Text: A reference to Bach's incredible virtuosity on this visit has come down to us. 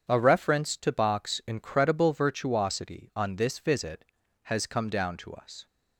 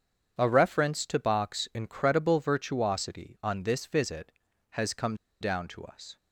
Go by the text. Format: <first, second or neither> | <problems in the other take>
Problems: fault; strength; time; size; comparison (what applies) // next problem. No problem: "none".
first | pauses between "come" and "down"; slight; at 5.1 s; 0.25 s long